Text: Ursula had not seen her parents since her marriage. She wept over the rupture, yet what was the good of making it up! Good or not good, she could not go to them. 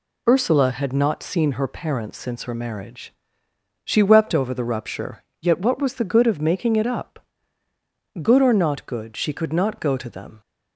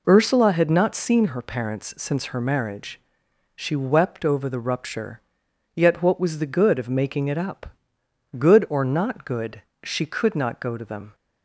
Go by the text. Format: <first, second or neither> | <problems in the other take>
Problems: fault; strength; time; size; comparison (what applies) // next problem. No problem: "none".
neither | none